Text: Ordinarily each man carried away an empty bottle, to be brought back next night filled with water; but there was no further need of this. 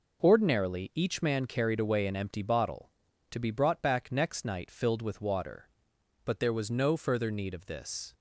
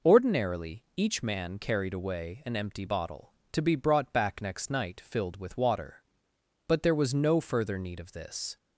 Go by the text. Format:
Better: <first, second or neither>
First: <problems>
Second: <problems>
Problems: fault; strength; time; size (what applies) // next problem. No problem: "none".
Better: neither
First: none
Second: none